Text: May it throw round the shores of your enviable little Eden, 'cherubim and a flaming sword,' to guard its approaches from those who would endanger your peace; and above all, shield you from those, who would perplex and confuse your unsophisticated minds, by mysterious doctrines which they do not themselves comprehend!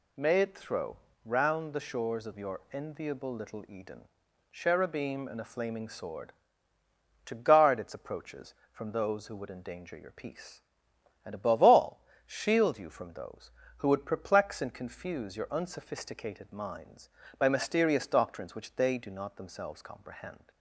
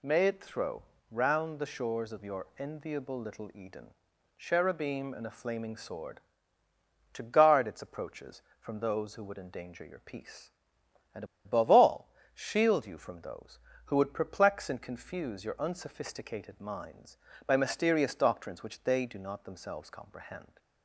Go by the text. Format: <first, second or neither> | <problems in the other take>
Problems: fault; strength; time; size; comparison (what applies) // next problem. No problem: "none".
first | pauses between "throw" and "round"; slight; at 0.8 s; 0.26 s long; slight in the first // pauses between "and" and "above"; slight; at 11.2 s; 0.21 s long